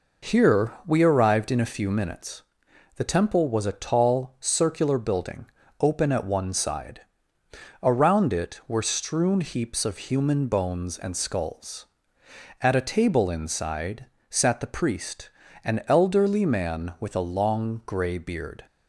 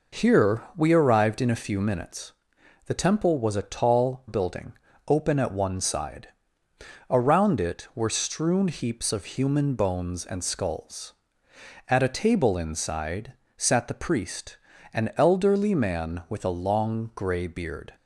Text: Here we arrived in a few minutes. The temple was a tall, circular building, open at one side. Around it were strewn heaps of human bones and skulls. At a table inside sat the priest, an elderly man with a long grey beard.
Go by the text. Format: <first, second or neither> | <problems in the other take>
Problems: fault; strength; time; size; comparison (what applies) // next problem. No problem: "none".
first | pauses between "Here" and "we"; slight; at 0.6 s; 0.16 s long; slight in the first // skips "circular"; at 4.2 s // pauses between "inside" and "sat"; slight; at 13.3 s; 0.24 s long; slight in the first